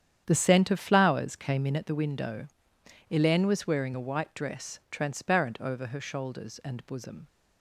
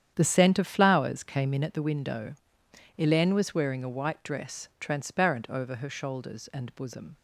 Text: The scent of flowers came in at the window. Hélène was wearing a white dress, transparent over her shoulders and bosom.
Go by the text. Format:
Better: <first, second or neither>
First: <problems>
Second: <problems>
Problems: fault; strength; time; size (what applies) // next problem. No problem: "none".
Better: neither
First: starts louder than the rest; strong; until 1.2 s; 9.5 dB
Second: starts louder than the rest; strong; until 1.1 s; 9.5 dB